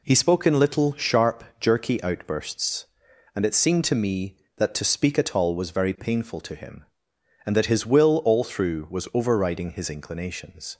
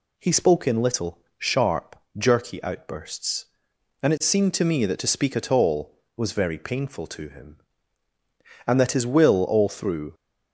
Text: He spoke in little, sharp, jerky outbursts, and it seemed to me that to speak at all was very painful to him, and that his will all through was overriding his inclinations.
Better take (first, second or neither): first